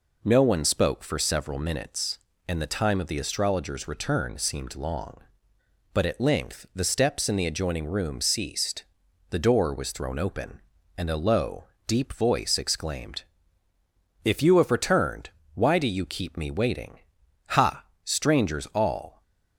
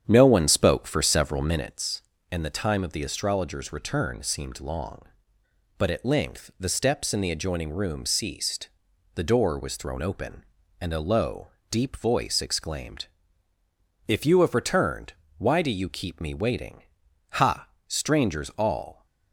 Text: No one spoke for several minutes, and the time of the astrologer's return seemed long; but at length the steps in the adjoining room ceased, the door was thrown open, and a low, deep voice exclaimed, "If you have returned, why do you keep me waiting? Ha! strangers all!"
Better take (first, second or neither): first